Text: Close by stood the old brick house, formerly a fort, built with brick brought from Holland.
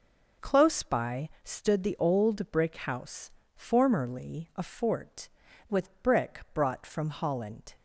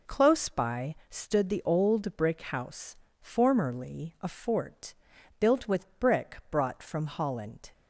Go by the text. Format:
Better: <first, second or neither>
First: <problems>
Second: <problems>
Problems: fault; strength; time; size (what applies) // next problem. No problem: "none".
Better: second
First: pauses between "by" and "stood"; slight; at 1.2 s; 0.16 s long // skips "built"; at 5.4 s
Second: pauses between "by" and "stood"; slight; at 0.9 s; 0.16 s long